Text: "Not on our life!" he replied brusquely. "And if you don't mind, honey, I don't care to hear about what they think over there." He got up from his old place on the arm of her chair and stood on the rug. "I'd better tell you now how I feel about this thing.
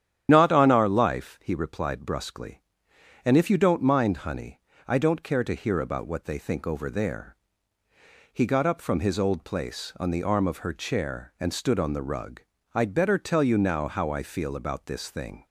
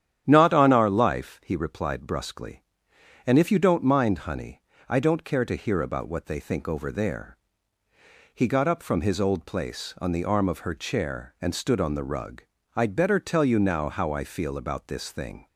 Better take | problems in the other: second | loses the start of "Not"; at 0.2 s; 35 ms // starts louder than the rest; strong; until 1.3 s; 10 dB; strong in the second

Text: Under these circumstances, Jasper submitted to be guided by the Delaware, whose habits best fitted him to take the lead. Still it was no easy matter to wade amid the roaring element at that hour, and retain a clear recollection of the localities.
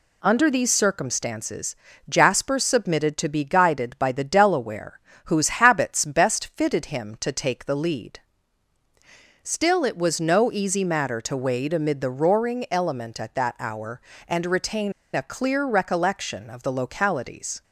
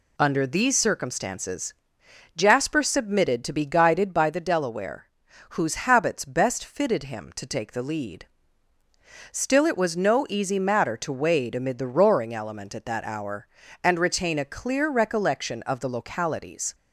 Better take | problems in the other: second | pauses between "retain" and "a"; slight; at 14.9 s; 0.22 s long

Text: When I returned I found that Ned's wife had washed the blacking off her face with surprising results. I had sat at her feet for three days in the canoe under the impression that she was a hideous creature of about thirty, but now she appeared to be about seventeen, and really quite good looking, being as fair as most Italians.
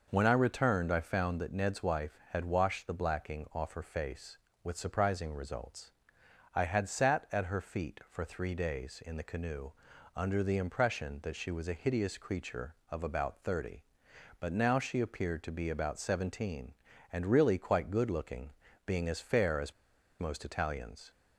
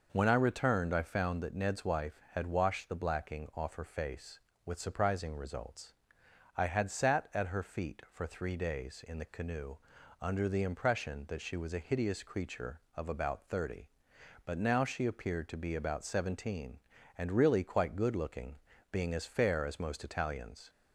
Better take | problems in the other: second | pauses between "canoe" and "under"; at 9.7 s; 0.44 s long; also in the second // pauses between "as" and "most"; noticeable; at 19.7 s; 0.47 s long

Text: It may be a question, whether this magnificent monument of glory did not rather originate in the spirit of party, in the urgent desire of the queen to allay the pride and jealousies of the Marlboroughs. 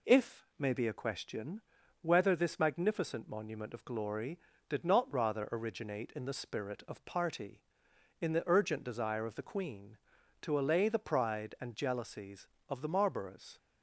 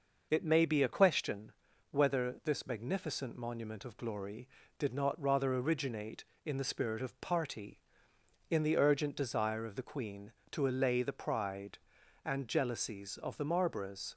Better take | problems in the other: second | says "If" for "It"; at 0.0 s

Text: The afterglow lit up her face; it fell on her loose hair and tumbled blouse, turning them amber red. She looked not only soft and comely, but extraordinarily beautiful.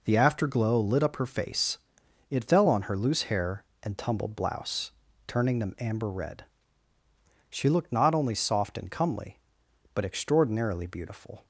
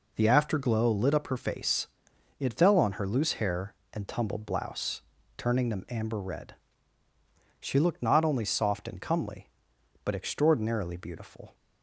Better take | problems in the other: neither | none

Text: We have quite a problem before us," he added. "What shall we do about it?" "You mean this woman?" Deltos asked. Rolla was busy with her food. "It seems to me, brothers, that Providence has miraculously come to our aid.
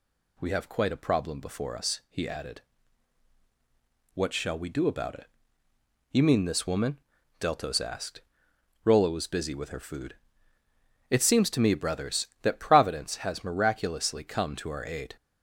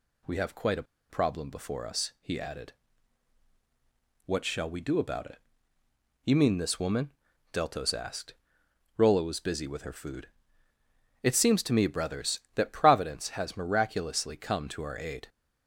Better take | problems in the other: first | pauses between "a" and "problem"; slight; at 0.8 s; 0.26 s long

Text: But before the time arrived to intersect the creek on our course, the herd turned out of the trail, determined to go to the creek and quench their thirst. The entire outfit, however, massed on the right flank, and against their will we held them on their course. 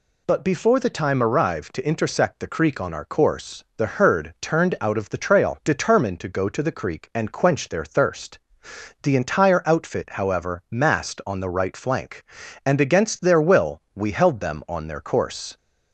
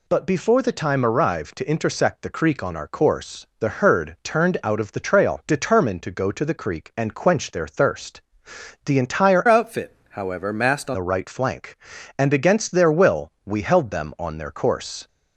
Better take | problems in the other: first | changes voice from "outfit" to "on"; from 9.4 to 10.9 s; 1.5 s long

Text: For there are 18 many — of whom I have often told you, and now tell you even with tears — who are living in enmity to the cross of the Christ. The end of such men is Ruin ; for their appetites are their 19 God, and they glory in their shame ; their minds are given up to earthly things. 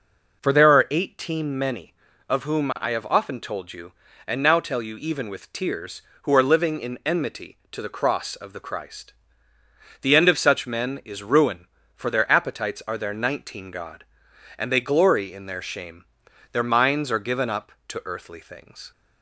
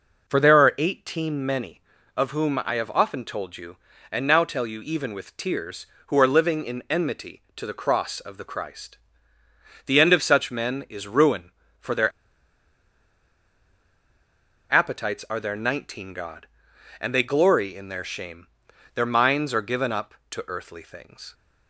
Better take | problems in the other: first | pauses between "their" and "appetites"; strong; at 12.1 s; 2.6 s long

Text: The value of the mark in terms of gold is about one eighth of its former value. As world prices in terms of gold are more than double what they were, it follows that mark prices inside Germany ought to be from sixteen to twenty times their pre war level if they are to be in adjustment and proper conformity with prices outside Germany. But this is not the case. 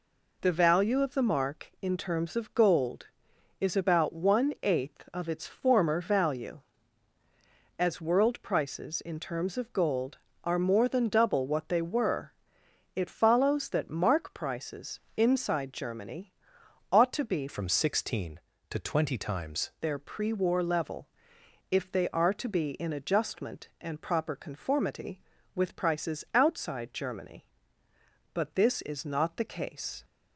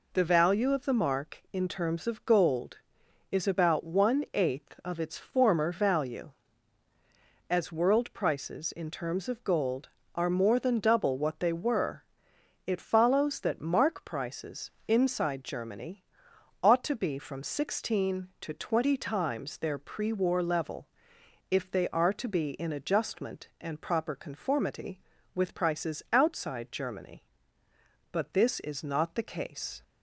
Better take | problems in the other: second | pauses between "prices" and "inside"; slight; at 15.0 s; 0.16 s long; slight in the second // pauses between "Germany" and "ought"; noticeable; at 16.3 s; 0.62 s long; noticeable in the second // changes voice from "from" to "times"; from 17.4 to 19.6 s; 2.2 s long // pauses between "level" and "if"; noticeable; at 21.0 s; 0.64 s long; noticeable in the second

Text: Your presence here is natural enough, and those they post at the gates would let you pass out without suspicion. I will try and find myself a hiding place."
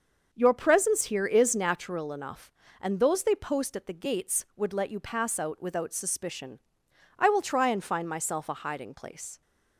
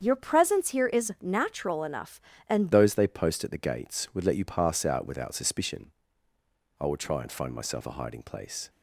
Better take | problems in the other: first | starts louder than the rest; strong; until 1.0 s; 7.5 dB; also in the first // changes voice at "those"; from 2.7 s on; 5.9 s long

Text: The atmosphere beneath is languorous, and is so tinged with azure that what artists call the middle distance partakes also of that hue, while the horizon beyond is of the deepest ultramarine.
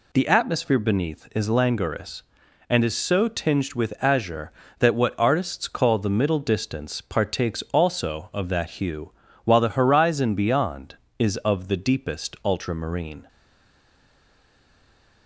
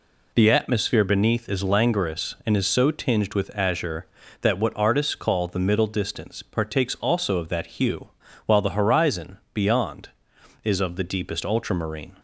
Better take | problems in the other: second | stays silent after the last word; noticeable; from 13.2 s on; 2.0 s long

